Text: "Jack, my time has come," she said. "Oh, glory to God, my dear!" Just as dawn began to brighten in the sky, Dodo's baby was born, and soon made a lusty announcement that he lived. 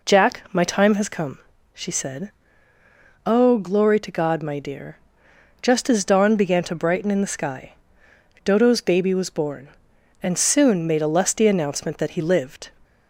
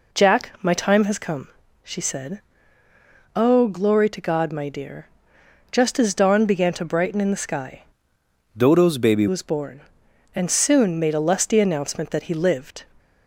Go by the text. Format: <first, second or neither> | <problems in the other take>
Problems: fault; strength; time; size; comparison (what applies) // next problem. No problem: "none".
first | changes voice from "Dodo's" to "baby"; from 8.5 to 9.2 s; 0.7 s long